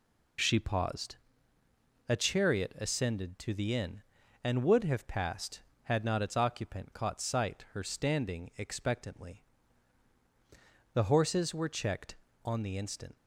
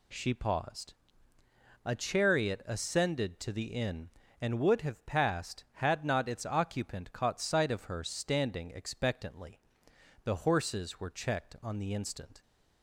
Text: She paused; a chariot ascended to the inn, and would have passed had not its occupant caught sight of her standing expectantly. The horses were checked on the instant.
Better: second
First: skips "of"; at 7.6 s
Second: none

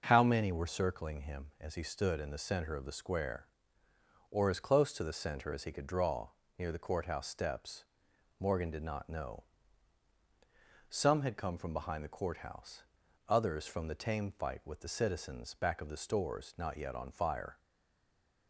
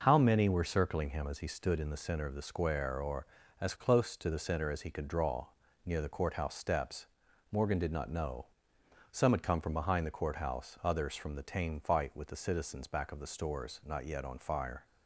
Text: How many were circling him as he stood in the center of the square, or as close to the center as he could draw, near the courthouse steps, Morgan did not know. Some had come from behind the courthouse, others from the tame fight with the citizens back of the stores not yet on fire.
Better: second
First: stays silent after the last word; slight; from 17.5 s on; 0.9 s long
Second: none

